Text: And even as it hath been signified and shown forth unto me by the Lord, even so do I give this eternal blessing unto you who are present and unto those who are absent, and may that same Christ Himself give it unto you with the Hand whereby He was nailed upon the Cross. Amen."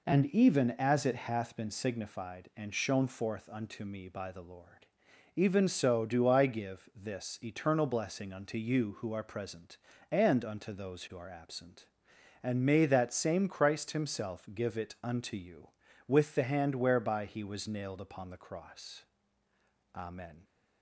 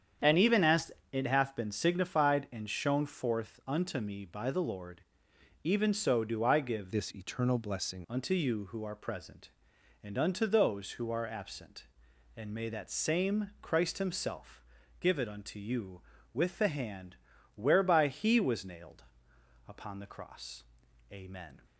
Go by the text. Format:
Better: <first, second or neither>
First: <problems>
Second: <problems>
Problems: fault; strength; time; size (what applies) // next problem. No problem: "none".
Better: first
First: none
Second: starts louder than the rest; strong; until 1.4 s; 8.5 dB // pauses between "as" and "it"; slight; at 0.9 s; 0.22 s long // changes voice from "this" to "blessing"; from 6.9 to 8.0 s; 1.1 s long // pauses between "Himself" and "give"; slight; at 14.6 s; 0.36 s long // pauses between "Hand" and "whereby"; at 17.1 s; 0.40 s long // pauses between "nailed" and "upon"; noticeable; at 19.0 s; 0.64 s long